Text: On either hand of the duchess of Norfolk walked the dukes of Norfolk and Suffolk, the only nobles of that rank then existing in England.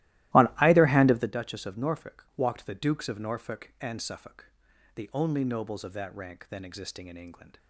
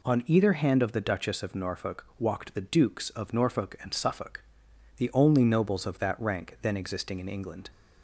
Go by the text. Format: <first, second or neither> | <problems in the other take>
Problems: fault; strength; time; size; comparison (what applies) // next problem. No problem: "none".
second | starts louder than the rest; strong; until 1.3 s; 16.5 dB